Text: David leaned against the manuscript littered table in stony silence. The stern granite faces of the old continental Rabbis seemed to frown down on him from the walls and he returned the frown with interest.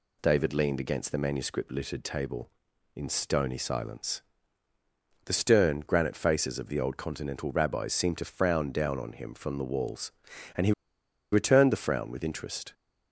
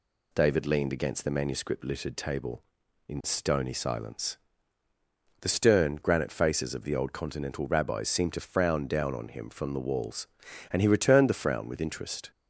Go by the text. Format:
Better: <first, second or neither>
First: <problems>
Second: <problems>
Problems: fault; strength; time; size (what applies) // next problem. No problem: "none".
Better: second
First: pauses between "he" and "returned"; noticeable; at 10.7 s; 0.59 s long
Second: none